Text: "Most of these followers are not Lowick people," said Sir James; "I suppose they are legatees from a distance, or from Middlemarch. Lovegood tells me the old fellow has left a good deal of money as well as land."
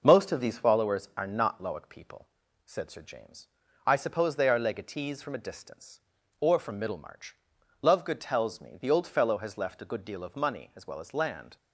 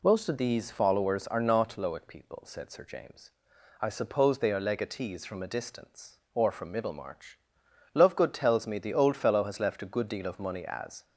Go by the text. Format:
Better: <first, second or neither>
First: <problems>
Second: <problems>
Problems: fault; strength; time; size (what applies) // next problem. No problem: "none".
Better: first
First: none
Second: stops before "well as land"; at 11.0 s